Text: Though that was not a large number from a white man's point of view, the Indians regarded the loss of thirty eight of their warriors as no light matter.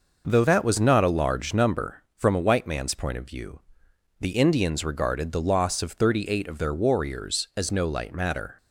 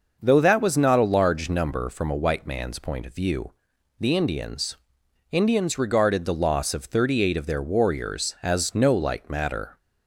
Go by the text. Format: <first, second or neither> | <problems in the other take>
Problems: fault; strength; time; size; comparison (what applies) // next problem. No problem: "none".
first | starts louder than the rest; noticeable; until 1.2 s; 6 dB // says "Indians" twice; at 5.3 s